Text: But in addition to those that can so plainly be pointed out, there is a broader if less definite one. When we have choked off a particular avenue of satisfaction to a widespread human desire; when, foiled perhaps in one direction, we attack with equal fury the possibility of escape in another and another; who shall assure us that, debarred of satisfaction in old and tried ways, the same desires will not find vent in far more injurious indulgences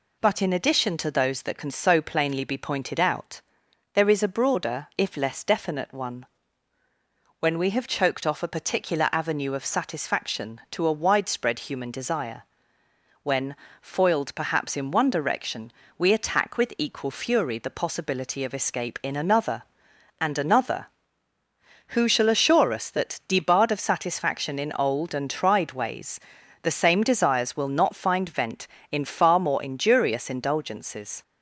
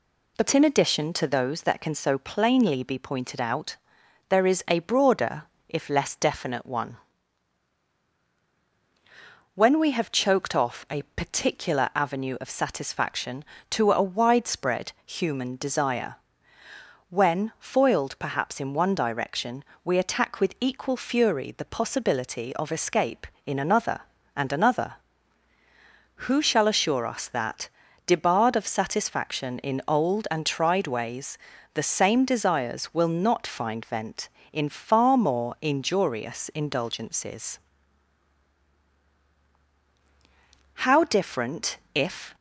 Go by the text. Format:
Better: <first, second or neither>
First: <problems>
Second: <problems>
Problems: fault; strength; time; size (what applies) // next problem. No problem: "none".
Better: first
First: none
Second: pauses between "broader" and "if"; slight; at 5.4 s; 0.26 s long // goes on to say "How different if"; from 40.8 s on; 1.5 s long